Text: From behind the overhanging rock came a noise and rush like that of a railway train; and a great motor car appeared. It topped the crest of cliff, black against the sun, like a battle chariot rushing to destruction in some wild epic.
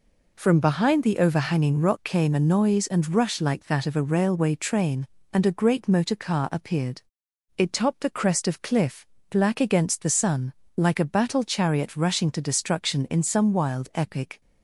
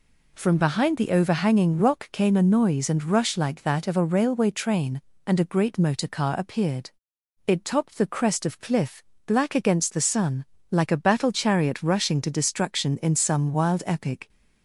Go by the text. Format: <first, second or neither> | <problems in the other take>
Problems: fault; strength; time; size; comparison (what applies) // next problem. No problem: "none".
neither | none